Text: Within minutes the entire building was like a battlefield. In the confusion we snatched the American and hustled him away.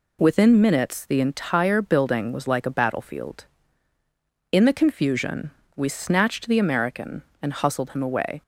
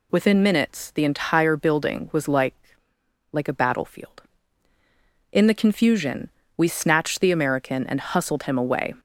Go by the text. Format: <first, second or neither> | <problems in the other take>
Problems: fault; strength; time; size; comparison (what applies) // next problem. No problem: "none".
first | says "like" twice; at 3.3 s // pauses between "confusion" and "we"; slight; at 6.2 s; 0.28 s long; slight in the first